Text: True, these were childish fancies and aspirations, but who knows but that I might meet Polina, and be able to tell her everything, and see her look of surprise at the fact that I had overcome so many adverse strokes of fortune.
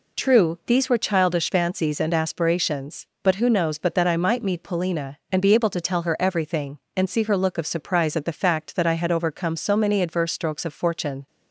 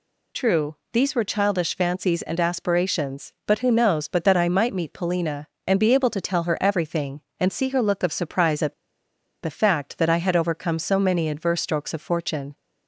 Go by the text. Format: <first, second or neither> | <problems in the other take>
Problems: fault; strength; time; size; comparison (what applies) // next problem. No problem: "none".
first | pauses between "at" and "the"; noticeable; at 8.7 s; 0.69 s long